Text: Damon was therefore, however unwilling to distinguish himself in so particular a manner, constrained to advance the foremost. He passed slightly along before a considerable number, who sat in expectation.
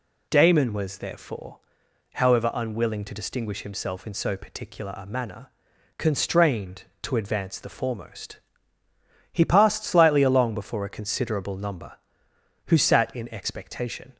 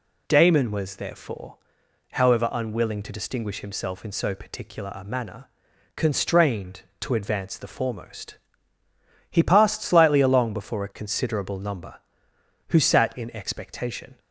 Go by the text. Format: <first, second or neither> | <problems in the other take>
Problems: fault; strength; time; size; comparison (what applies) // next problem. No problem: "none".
neither | none